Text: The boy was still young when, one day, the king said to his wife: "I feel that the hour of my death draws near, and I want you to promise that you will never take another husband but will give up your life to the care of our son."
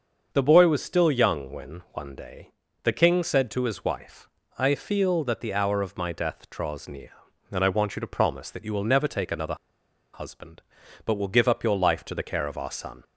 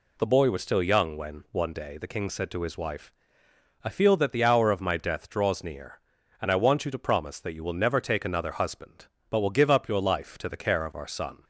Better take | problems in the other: second | starts louder than the rest; until 1.3 s; 6.5 dB // pauses between "another" and "husband"; noticeable; at 9.5 s; 0.58 s long

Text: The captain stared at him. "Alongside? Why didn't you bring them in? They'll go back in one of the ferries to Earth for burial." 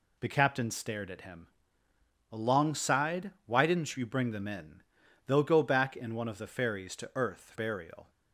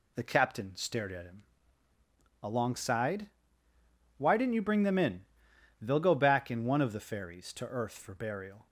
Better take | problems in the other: second | skips "for"; at 7.5 s

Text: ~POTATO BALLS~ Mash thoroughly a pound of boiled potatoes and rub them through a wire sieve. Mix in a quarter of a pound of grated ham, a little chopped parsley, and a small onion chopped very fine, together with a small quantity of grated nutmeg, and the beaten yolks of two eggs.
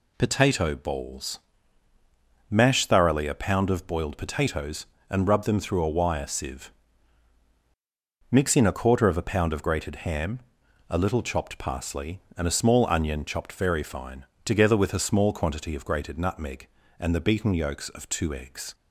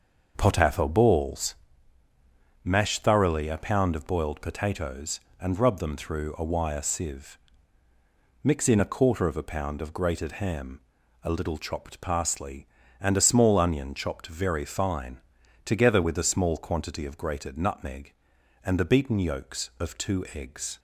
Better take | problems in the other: first | starts louder than the rest; until 1.7 s; 6.5 dB

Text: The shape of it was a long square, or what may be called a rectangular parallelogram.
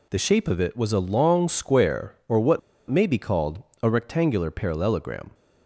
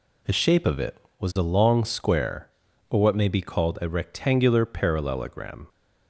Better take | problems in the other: second | pauses between "what" and "may"; slight; at 2.5 s; 0.30 s long // pauses between "called" and "a"; slight; at 3.6 s; 0.22 s long

